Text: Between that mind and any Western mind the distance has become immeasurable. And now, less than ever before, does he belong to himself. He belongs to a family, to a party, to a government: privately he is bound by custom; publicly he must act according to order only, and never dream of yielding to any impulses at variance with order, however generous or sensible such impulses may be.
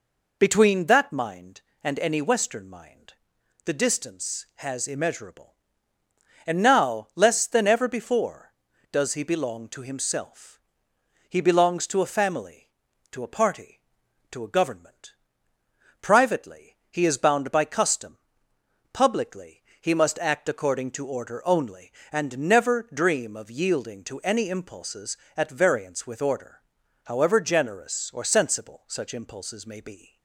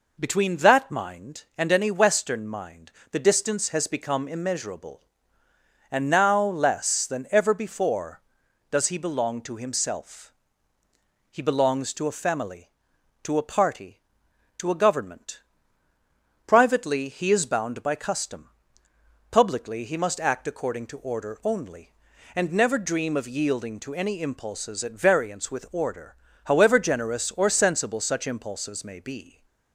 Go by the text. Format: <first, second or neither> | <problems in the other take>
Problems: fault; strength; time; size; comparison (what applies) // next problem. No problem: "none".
second | pauses between "mind" and "the"; noticeable; at 3.1 s; 0.52 s long; slight in the second // skips "become"; at 4.8 s // pauses between "privately" and "he"; slight; at 16.7 s; 0.16 s long // pauses between "publicly" and "he"; slight; at 19.6 s; 0.18 s long